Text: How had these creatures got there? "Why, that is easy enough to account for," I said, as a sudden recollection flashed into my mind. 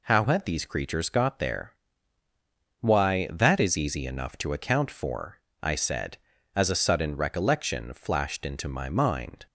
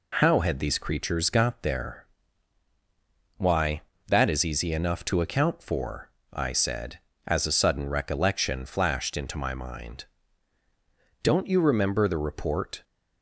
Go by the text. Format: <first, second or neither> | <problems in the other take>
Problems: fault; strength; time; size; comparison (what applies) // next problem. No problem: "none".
first | goes on to say "Don't you remember the report"; from 11.2 s on; 1.6 s long